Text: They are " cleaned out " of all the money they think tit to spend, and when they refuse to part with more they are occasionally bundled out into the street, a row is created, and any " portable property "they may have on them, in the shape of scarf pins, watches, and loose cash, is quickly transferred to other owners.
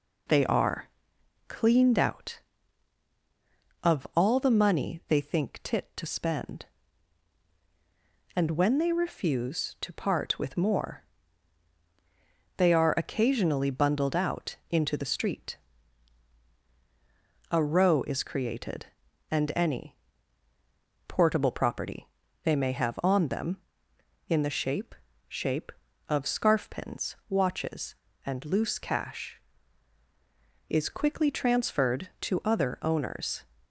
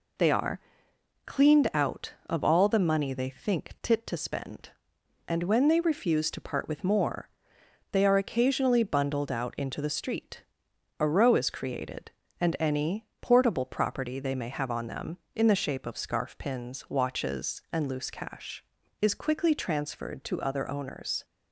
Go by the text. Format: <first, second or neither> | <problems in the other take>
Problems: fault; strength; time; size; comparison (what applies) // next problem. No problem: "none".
second | pauses between "more" and "they"; strong; at 11.0 s; 1.5 s long; noticeable in the second // pauses between "property" and "they"; slight; at 22.0 s; 0.34 s long // says "shape" twice; at 25.2 s